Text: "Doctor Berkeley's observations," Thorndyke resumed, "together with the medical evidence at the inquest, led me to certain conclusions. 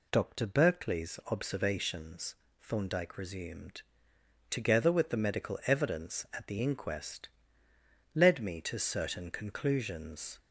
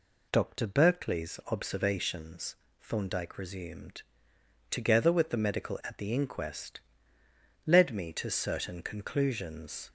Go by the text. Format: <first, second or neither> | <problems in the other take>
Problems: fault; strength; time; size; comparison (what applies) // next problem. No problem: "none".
first | skips "evidence"; at 5.8 s